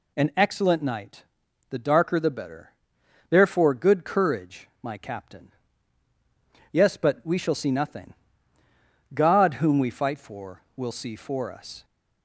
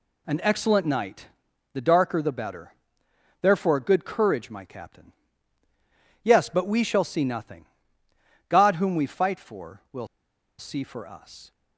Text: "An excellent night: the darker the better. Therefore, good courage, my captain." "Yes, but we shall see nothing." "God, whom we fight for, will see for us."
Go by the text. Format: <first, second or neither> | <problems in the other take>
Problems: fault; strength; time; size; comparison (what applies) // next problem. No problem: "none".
first | pauses between "will" and "see"; noticeable; at 10.0 s; 0.52 s long